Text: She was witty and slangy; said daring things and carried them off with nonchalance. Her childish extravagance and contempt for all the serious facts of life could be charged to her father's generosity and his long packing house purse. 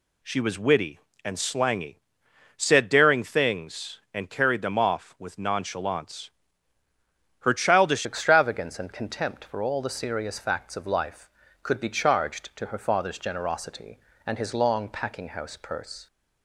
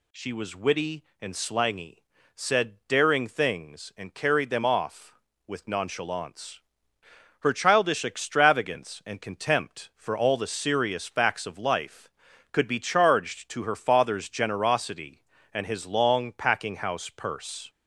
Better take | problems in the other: second | changes voice at "extravagance"; from 8.0 s on; 8.0 s long

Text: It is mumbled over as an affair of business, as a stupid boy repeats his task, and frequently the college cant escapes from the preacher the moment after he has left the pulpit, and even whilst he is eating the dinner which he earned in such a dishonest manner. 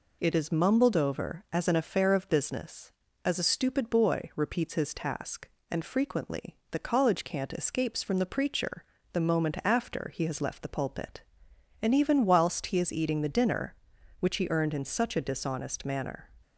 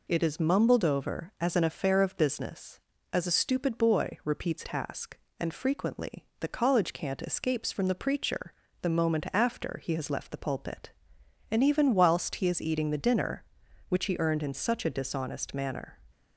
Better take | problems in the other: first | skips "his"; at 4.6 s // pauses between "preacher" and "the"; slight; at 8.5 s; 0.28 s long; slight in the first

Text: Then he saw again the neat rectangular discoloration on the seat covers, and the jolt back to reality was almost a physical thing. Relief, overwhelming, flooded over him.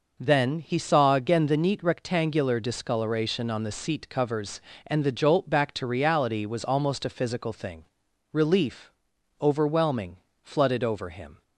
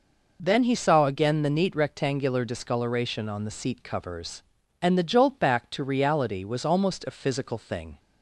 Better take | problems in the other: first | stops before "Relief overwhelming flooded over him"; at 7.9 s

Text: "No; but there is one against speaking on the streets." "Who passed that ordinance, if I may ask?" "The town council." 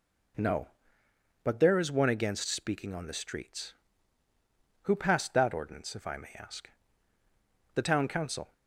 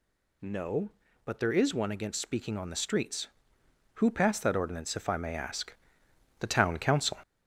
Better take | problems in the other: first | gets louder; noticeable; throughout; 5 dB

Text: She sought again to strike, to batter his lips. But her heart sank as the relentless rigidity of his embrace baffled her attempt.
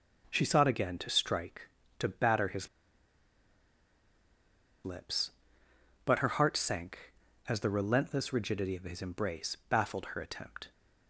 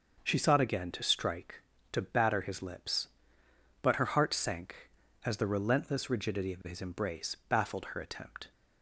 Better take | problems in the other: second | starts louder than the rest; noticeable; until 1.3 s; 6 dB; noticeable in the second // pauses between "his" and "lips"; strong; at 2.6 s; 2.1 s long

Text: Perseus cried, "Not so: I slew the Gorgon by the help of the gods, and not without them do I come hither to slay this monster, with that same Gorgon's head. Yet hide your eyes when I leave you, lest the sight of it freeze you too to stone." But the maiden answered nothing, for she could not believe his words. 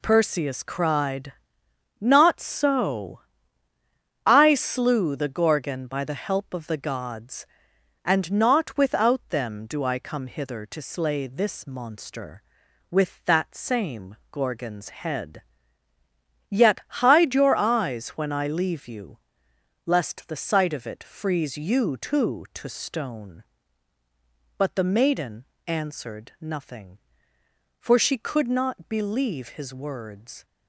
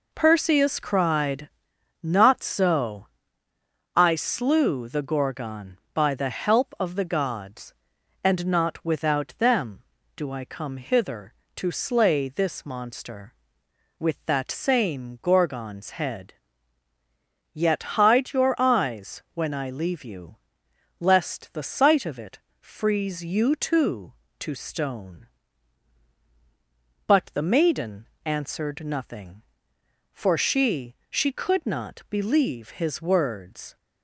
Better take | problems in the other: first | pauses between "it" and "freeze"; slight; at 22.3 s; 0.22 s long // pauses between "maiden" and "answered"; slight; at 28.0 s; 0.16 s long; slight in the first // says "she" twice; at 31.0 s

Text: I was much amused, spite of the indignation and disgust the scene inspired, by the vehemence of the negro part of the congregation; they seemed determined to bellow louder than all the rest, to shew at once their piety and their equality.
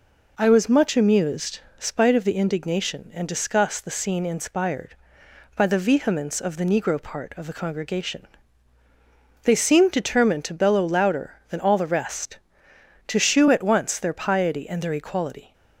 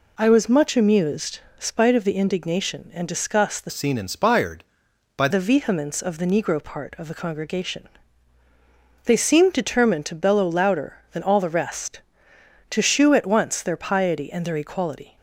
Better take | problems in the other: first | changes voice from "scene" to "by"; from 3.7 to 5.2 s; 1.5 s long

